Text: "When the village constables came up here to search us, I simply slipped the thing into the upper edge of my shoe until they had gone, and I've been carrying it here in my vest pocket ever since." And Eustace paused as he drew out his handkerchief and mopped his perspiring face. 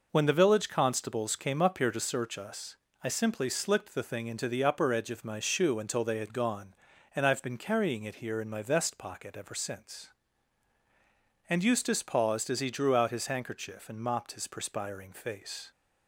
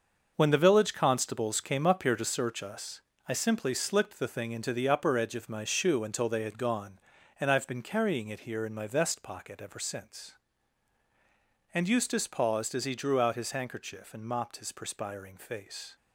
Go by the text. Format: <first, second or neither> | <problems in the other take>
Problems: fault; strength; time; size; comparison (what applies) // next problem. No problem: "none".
first | gets quieter; strong; throughout; 9 dB